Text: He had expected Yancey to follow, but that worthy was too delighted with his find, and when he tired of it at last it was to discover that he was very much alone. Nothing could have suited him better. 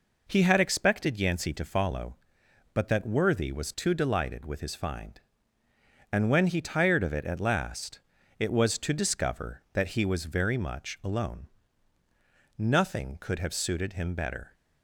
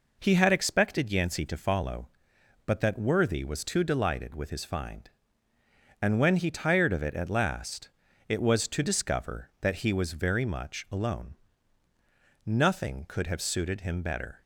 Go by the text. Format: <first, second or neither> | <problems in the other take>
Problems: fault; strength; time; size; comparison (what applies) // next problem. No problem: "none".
neither | pauses between "last" and "it"; the same in both